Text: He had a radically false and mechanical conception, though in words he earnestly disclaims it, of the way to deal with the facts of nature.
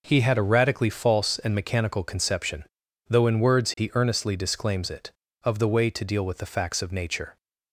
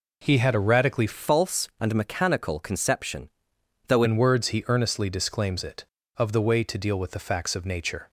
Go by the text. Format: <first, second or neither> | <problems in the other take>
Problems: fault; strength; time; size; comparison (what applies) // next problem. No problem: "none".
first | changes voice from "false" to "though"; from 1.1 to 4.0 s; 2.9 s long